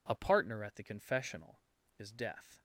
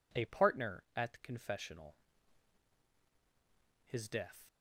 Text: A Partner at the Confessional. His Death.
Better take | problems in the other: second | says "Is" for "His"; at 1.9 s

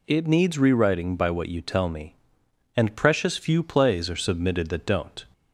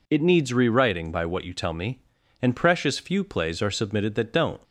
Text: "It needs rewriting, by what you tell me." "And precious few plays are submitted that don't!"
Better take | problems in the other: neither | none

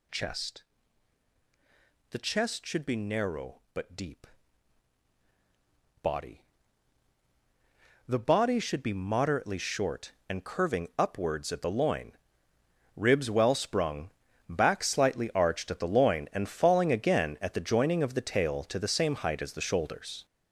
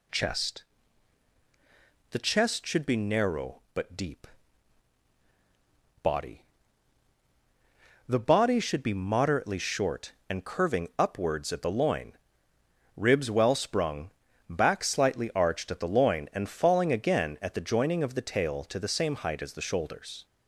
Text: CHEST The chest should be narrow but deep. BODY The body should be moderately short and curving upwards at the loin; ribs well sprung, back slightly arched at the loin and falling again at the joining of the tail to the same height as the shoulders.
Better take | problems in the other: second | gets louder; strong; throughout; 8.5 dB // pauses between "CHEST" and "The"; strong; at 0.6 s; 1.4 s long; strong in the second // pauses between "BODY" and "The"; strong; at 6.4 s; 1.6 s long; strong in the second

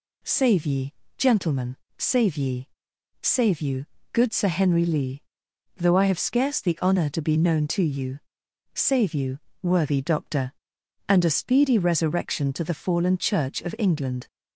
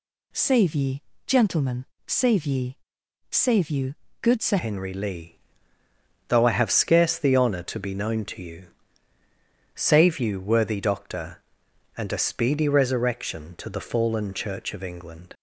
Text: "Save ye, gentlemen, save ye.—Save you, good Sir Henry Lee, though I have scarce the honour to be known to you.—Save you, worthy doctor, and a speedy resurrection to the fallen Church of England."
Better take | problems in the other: first | changes voice at "Henry"; from 4.5 s on; 10.8 s long

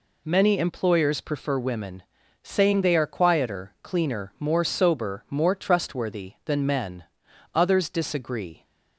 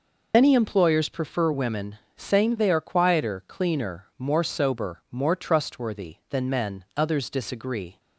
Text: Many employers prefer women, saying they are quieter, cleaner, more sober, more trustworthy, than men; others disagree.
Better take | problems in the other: first | loses the start of "Many"; at 0.3 s; 95 ms

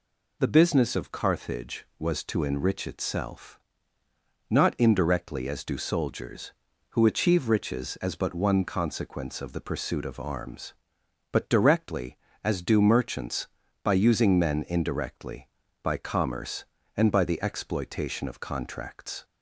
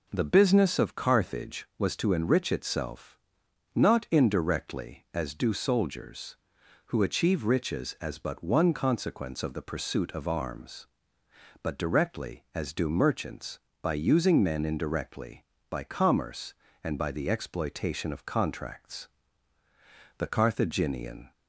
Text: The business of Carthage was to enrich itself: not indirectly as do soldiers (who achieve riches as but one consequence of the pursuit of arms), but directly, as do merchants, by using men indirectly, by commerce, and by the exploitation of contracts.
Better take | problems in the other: first | goes on to say "The Carthaginian"; noticeable; from 20.1 s on; 1.1 s long

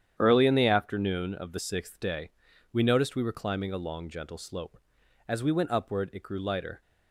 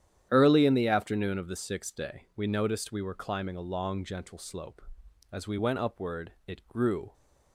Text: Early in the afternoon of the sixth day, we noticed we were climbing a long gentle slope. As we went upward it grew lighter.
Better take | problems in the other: first | starts louder than the rest; strong; until 1.3 s; 10.5 dB; strong in the first // stops before "lighter"; at 7.1 s

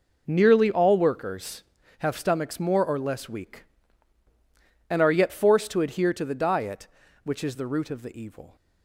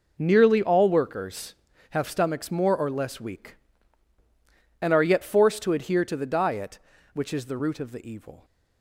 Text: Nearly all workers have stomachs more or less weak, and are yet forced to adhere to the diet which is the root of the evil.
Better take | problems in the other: neither | none

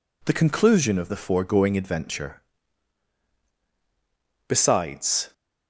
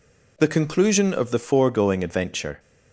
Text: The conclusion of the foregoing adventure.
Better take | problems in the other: second | goes on to say "Besides"; noticeable; from 4.4 s on; 0.86 s long

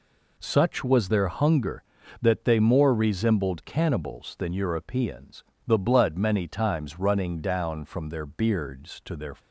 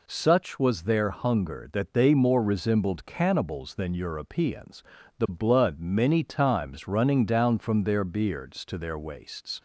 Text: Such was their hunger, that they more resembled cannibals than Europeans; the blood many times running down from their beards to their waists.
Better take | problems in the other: second | stops before "waists"; at 9.3 s

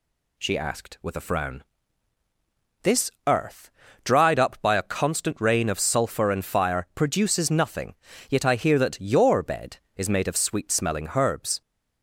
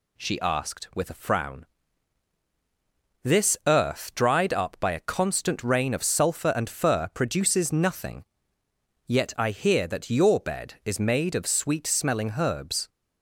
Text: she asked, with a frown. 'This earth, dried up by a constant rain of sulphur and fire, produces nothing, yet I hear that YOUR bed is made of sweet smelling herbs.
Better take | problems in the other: first | says "fur" for "fire"; at 6.6 s

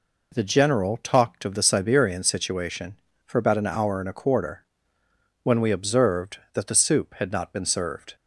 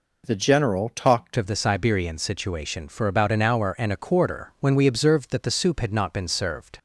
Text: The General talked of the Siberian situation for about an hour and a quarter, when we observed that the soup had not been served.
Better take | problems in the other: first | changes voice at "of"; from 1.3 s on; 5.4 s long

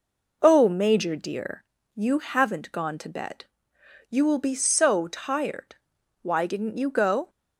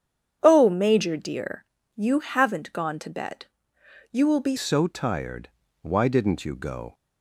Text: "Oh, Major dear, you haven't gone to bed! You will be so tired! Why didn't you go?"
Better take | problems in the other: first | starts louder than the rest; strong; until 1.4 s; 8.5 dB // changes voice at "so"; from 4.5 s on; 2.4 s long

